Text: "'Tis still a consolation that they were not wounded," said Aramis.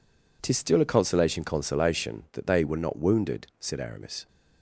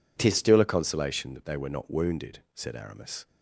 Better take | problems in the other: second | says "consolation" twice; at 1.4 s

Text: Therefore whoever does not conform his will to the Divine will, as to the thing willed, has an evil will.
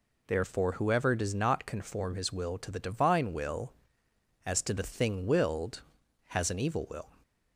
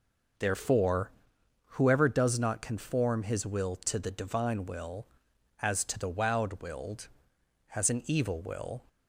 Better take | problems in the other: first | pauses between "Therefore" and "whoever"; noticeable; at 1.0 s; 0.60 s long // says "wowed" for "thing"; at 6.0 s

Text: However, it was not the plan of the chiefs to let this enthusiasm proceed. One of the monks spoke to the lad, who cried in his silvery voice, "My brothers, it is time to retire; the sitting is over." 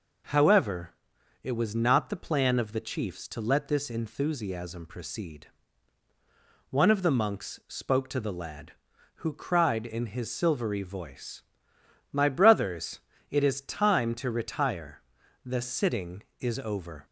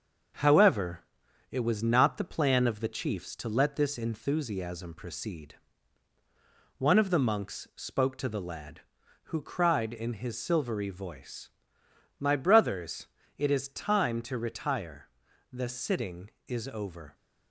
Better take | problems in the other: first | gets quieter; noticeable; throughout; 5 dB

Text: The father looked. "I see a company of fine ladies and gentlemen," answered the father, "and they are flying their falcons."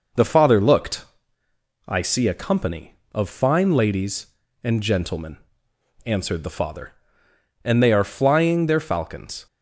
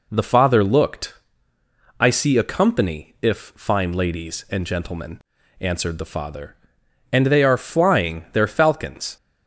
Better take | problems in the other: first | says "if" for "of"; at 3.2 s

